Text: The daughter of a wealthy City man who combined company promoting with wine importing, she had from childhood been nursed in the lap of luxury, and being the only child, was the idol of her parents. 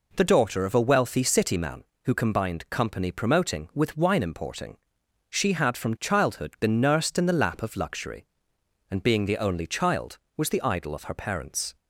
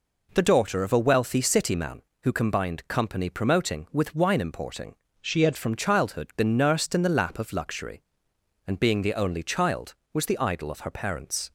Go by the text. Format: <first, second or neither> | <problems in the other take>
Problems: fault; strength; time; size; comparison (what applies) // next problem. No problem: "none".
first | changes voice from "she" to "had"; from 5.2 to 5.5 s; 0.3 s long